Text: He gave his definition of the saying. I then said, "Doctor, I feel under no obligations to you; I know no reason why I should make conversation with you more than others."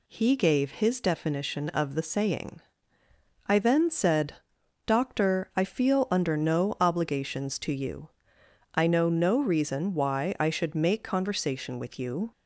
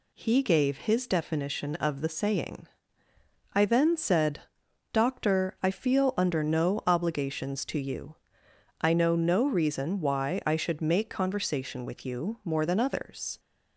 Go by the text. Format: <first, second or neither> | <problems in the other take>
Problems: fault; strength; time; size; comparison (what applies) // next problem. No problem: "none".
second | stops before "more than others"; at 12.3 s